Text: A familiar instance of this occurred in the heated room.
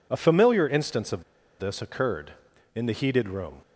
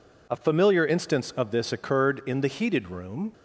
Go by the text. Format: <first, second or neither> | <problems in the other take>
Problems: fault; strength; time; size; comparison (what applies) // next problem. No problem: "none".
second | pauses between "of" and "this"; at 1.2 s; 0.36 s long